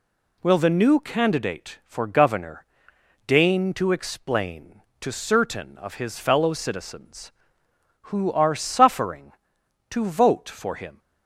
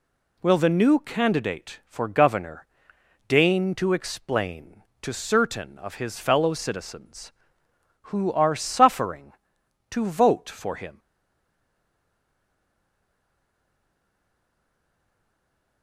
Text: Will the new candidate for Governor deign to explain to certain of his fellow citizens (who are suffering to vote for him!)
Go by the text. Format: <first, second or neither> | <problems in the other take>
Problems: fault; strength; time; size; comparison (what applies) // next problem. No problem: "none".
first | pauses between "Governor" and "deign"; noticeable; at 2.6 s; 0.62 s long; noticeable in the first // stays silent after the last word; strong; from 10.9 s on; 4.9 s long